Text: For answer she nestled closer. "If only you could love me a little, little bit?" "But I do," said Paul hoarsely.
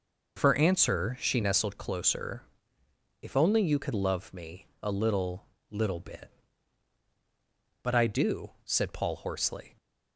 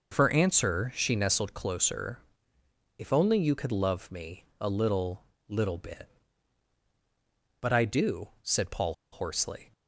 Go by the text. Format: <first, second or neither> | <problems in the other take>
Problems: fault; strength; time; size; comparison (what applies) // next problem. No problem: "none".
first | pauses between "me" and "a"; slight; at 4.4 s; 0.16 s long; slight in the first // pauses between "Paul" and "hoarsely"; slight; at 8.9 s; 0.19 s long